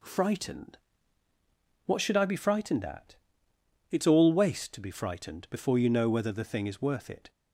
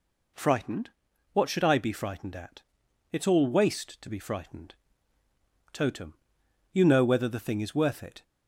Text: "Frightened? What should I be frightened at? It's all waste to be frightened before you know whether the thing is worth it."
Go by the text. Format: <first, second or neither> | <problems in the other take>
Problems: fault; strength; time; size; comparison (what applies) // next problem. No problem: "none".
first | says "totem" for "before"; at 5.7 s